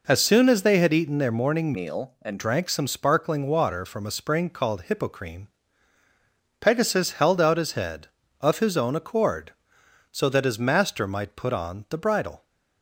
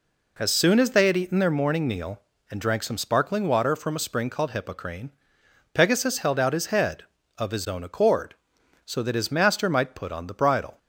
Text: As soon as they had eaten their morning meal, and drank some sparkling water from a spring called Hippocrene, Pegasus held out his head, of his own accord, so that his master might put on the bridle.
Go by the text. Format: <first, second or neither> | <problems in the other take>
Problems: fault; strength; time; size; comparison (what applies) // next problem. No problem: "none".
second | changes voice from "meal" to "and"; from 1.7 to 2.3 s; 0.6 s long